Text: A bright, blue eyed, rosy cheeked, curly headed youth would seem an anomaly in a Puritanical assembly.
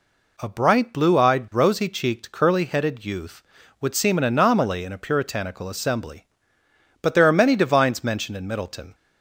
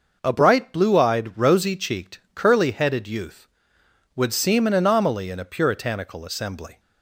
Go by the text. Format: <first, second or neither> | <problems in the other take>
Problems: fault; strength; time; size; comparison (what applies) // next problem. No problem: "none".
second | goes on to say "But there are many Divines mentioned in Middleton"; strong; from 7.0 s on; 1.9 s long